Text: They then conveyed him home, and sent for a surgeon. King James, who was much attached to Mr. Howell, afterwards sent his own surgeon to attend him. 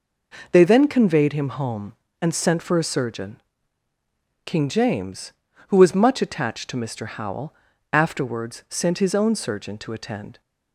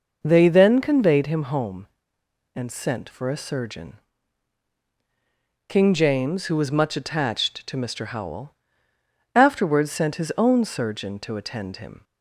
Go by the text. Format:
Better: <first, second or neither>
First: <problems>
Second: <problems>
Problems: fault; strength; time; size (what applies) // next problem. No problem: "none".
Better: second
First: stops before "him"; at 10.4 s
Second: none